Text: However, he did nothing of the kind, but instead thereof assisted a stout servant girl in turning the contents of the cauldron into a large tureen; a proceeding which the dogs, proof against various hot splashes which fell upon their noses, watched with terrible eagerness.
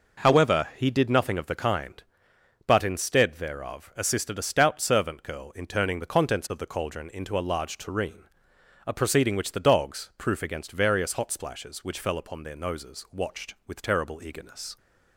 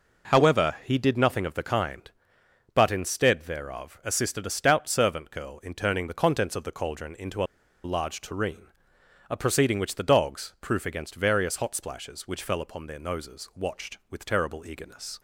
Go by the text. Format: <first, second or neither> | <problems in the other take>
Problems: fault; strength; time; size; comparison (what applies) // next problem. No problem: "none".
first | pauses between "into" and "a"; at 7.4 s; 0.40 s long